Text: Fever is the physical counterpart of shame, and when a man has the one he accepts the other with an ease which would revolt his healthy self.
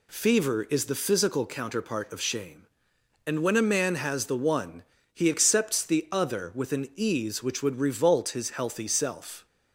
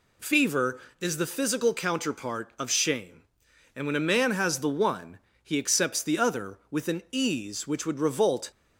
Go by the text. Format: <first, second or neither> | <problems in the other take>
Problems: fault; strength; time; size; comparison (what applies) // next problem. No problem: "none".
first | pauses between "one" and "he"; slight; at 5.1 s; 0.24 s long; slight in the first // stops before "his healthy self"; at 8.5 s